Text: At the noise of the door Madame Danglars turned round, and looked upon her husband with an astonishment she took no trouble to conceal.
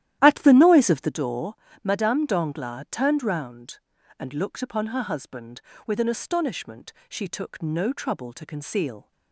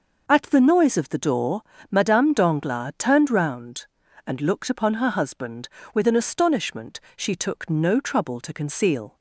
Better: second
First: starts louder than the rest; strong; until 1.2 s; 12.5 dB // pauses between "door" and "Madame"; slight; at 1.5 s; 0.26 s long // pauses between "astonishment" and "she"; slight; at 6.9 s; 0.18 s long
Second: pauses between "door" and "Madame"; slight; at 1.6 s; 0.26 s long // pauses between "astonishment" and "she"; slight; at 6.9 s; 0.18 s long

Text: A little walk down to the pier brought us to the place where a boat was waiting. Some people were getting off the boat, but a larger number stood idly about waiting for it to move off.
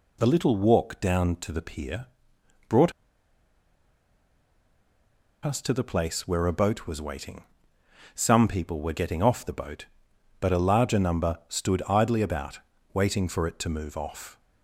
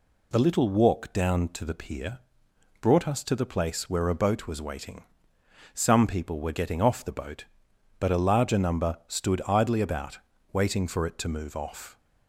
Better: second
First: pauses between "pier" and "brought"; noticeable; at 2.0 s; 0.60 s long // pauses between "brought" and "us"; strong; at 2.9 s; 2.5 s long // pauses between "about" and "waiting"; slight; at 12.5 s; 0.34 s long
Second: pauses between "pier" and "brought"; noticeable; at 2.1 s; 0.60 s long // pauses between "about" and "waiting"; slight; at 10.1 s; 0.34 s long

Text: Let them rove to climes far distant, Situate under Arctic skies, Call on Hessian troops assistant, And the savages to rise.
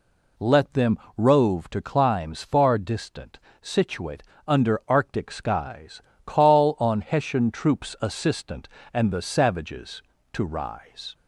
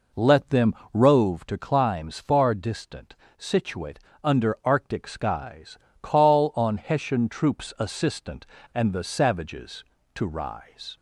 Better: first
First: pauses between "them" and "rove"; slight; at 0.9 s; 0.18 s long // pauses between "Situate" and "under"; slight; at 4.2 s; 0.24 s long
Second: starts louder than the rest; noticeable; until 1.4 s; 4.5 dB // pauses between "them" and "rove"; slight; at 0.7 s; 0.18 s long // pauses between "Situate" and "under"; slight; at 3.9 s; 0.24 s long

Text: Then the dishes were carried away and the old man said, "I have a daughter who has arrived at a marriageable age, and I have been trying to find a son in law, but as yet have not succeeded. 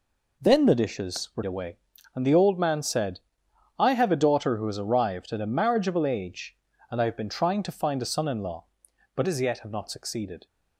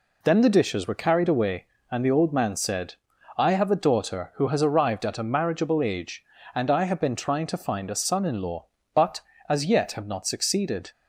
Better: second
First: skips "carried"; at 1.4 s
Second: none

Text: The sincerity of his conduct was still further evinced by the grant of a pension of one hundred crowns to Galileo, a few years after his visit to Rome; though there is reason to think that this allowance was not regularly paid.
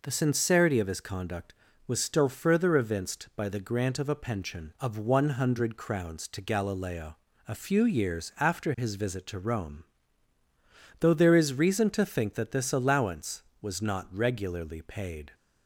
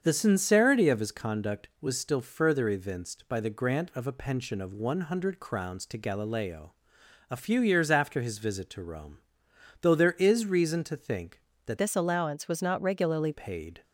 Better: first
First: none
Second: starts louder than the rest; strong; until 1.0 s; 7 dB // changes voice from "this" to "regularly"; from 11.7 to 13.3 s; 1.6 s long

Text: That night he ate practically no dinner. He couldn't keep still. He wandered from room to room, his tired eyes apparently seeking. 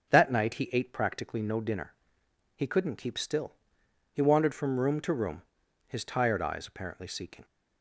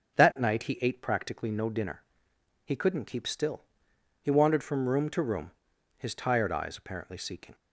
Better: neither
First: starts louder than the rest; until 1.1 s; 6.5 dB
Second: starts louder than the rest; until 1.2 s; 7 dB

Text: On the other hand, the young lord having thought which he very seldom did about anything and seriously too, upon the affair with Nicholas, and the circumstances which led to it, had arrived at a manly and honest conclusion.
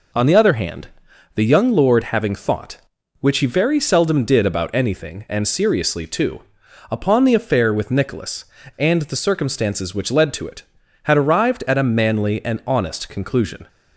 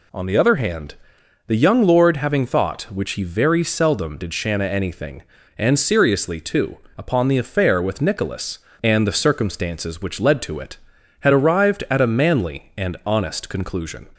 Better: first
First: none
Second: says "shanna" for "about"; at 4.3 s

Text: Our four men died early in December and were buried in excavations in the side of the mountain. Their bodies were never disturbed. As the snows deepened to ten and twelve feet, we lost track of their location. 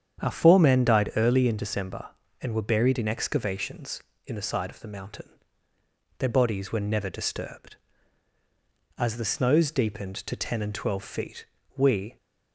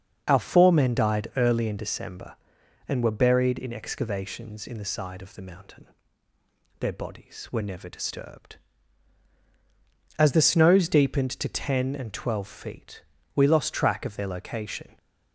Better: second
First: starts louder than the rest; strong; until 1.2 s; 8 dB // stops before "lost track of their location"; at 12.1 s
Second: starts louder than the rest; until 1.2 s; 6.5 dB

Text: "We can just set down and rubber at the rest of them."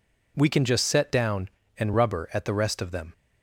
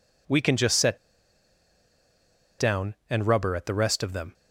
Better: first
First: none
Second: pauses between "set" and "down"; strong; at 0.9 s; 1.6 s long

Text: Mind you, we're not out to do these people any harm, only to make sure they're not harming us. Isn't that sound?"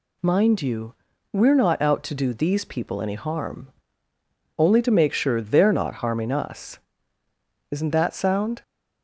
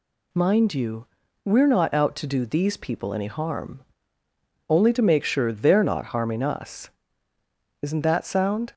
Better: neither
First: none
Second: none

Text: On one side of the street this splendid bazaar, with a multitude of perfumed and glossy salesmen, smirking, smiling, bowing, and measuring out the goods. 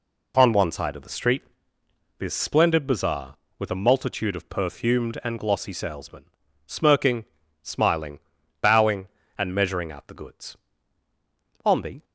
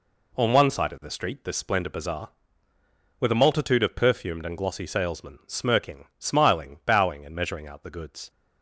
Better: second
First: pauses between "street" and "this"; noticeable; at 1.4 s; 0.76 s long // goes on to say "On the"; slight; from 11.6 s on; 0.40 s long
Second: none

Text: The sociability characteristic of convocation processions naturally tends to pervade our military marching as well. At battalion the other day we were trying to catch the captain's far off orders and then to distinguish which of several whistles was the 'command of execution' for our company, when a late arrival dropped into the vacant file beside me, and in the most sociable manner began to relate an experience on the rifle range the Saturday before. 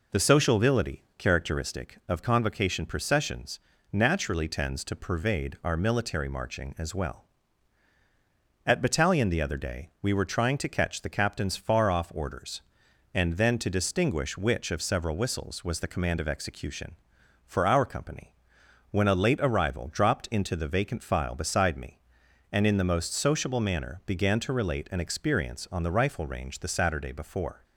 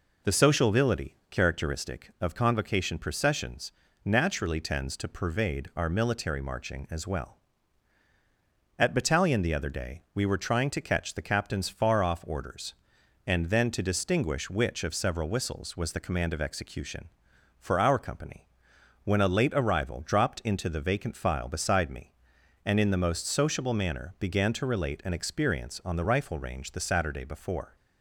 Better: neither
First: pauses between "processions" and "naturally"; slight; at 3.5 s; 0.32 s long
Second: pauses between "processions" and "naturally"; slight; at 3.7 s; 0.32 s long

